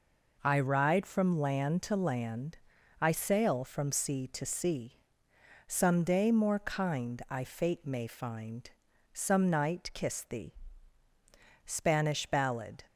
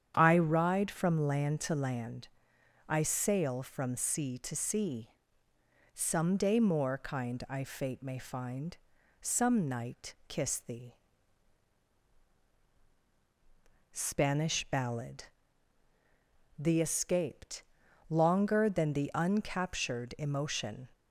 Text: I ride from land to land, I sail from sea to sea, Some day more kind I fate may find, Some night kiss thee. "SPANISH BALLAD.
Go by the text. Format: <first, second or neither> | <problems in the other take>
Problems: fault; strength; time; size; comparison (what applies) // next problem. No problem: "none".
first | starts louder than the rest; strong; until 1.1 s; 8.5 dB // goes on to say "THE escaped longer than the uncaptured emotion"; strong; from 16.5 s on; 4.3 s long